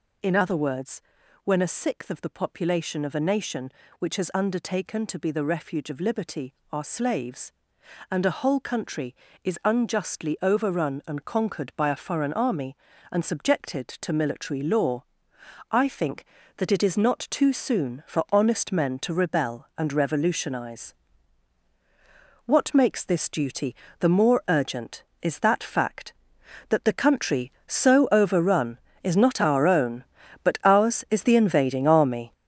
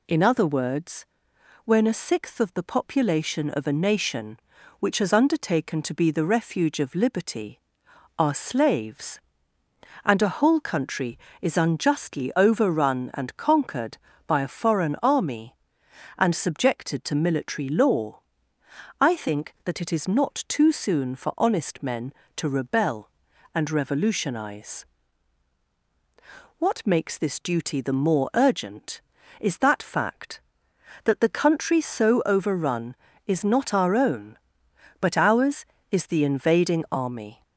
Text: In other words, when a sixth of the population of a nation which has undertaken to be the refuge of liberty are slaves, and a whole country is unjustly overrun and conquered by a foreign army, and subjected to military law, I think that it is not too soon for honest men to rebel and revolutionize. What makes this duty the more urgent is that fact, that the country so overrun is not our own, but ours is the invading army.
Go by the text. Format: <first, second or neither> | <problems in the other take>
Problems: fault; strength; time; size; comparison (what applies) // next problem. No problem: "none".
second | gets louder; throughout; 7 dB // pauses between "duty" and "the"; slight; at 23.7 s; 0.26 s long